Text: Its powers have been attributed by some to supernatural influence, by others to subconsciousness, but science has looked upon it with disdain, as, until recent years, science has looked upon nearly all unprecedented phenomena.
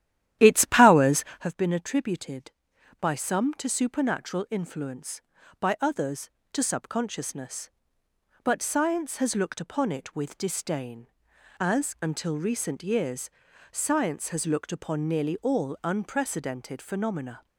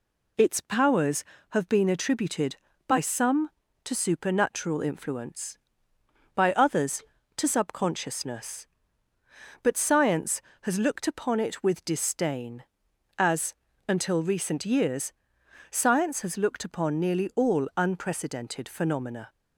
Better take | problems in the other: second | starts louder than the rest; strong; until 1.5 s; 12 dB

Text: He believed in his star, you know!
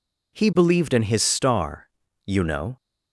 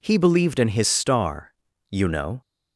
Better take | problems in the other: neither | none

